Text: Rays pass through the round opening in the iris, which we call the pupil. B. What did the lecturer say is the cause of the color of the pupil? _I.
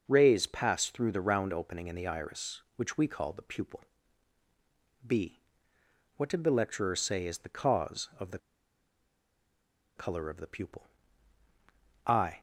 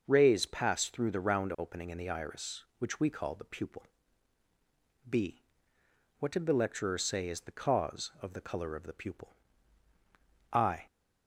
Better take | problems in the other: second | pauses between "the" and "color"; strong; at 8.3 s; 1.5 s long

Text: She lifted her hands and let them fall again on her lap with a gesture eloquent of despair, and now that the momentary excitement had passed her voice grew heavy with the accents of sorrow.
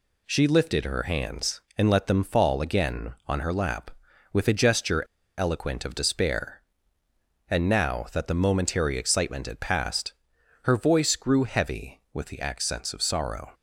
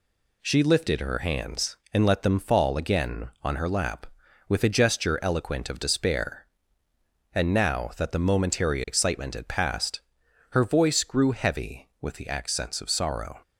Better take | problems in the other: second | pauses between "gesture" and "eloquent"; slight; at 5.0 s; 0.33 s long // pauses between "passed" and "her"; noticeable; at 10.1 s; 0.50 s long; noticeable in the second

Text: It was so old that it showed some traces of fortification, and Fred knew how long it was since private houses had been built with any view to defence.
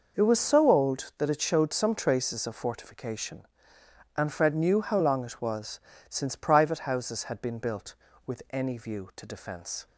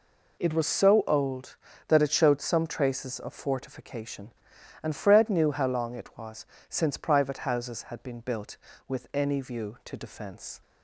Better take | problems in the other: neither | pauses between "was" and "since"; slight; the same in both

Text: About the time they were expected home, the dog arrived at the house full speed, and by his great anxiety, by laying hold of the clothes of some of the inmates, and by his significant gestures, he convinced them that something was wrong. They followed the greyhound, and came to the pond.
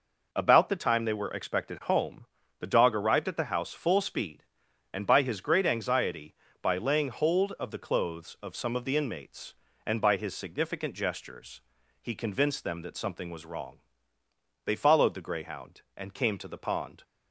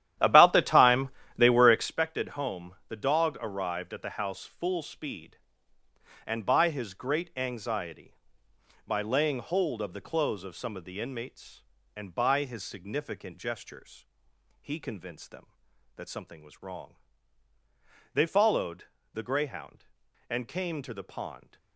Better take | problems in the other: first | starts louder than the rest; strong; until 2.0 s; 11.5 dB // pauses between "time" and "they"; slight; at 1.0 s; 0.26 s long // pauses between "followed" and "the"; slight; at 18.8 s; 0.30 s long

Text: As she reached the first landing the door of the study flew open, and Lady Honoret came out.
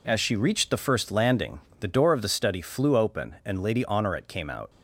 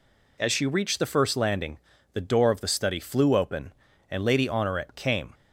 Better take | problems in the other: first | pauses between "landing" and "the"; slight; at 1.7 s; 0.36 s long; slight in the first // stops before "out"; at 5.3 s

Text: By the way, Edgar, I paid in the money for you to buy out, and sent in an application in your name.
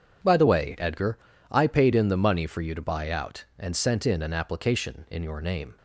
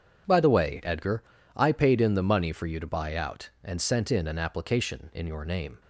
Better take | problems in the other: neither | none

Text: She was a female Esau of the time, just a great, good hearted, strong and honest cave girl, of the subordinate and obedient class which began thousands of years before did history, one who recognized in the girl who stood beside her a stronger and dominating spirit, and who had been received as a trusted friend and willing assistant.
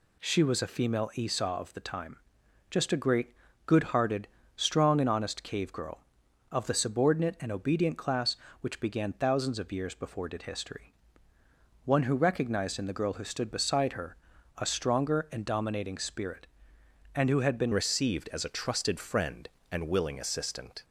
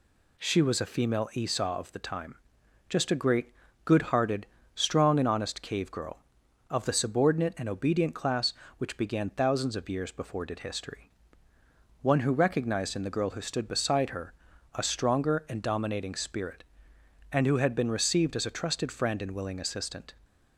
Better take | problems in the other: second | pauses between "her" and "a"; at 14.1 s; 0.40 s long; also in the second // changes voice at "received"; from 17.7 s on; 3.1 s long

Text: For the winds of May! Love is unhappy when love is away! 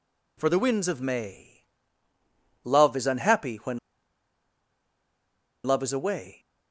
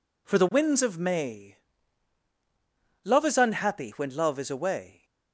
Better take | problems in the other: second | pauses between "when" and "love"; strong; at 3.7 s; 1.8 s long

